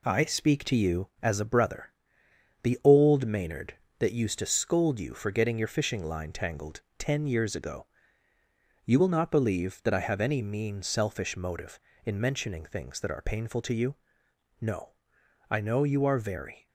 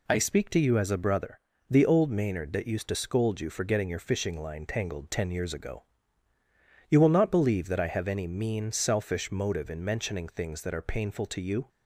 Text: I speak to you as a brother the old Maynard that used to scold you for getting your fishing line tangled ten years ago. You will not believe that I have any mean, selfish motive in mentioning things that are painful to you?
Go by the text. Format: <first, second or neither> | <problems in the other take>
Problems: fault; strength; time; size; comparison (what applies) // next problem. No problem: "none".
second | pauses between "brother" and "the"; noticeable; at 1.9 s; 0.70 s long; slight in the second // pauses between "tangled" and "ten"; slight; at 6.8 s; 0.18 s long // goes on to say "No I know you are very"; strong; from 14.5 s on; 2.0 s long